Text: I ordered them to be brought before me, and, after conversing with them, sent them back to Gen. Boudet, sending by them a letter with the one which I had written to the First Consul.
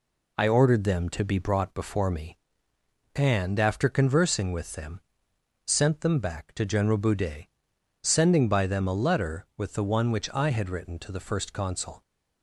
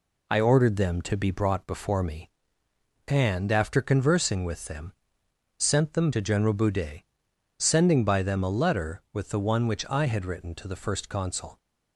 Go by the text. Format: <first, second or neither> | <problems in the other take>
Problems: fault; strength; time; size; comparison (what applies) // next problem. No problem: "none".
first | skips "back"; at 6.1 s